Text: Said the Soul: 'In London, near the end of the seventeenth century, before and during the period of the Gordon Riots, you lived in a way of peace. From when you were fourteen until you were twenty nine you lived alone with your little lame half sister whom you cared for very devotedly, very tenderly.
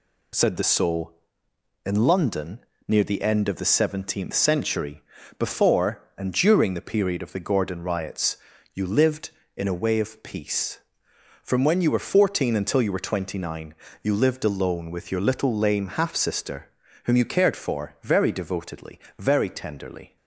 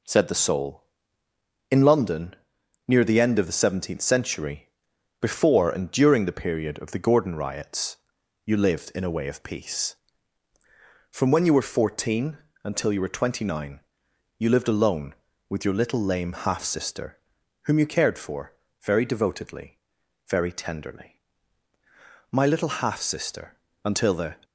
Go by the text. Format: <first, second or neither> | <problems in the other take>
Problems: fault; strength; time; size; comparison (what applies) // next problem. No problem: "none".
first | pauses between "fourteen" and "until"; slight; at 12.3 s; 0.28 s long // pauses between "nine" and "you"; noticeable; at 13.7 s; 0.60 s long; slight in the first // pauses between "sister" and "whom"; noticeable; at 17.1 s; 0.46 s long; slight in the first // pauses between "for" and "very"; slight; at 18.5 s; 0.28 s long // goes on to say "My little half sister Until the"; strong; from 22.2 s on; 2.0 s long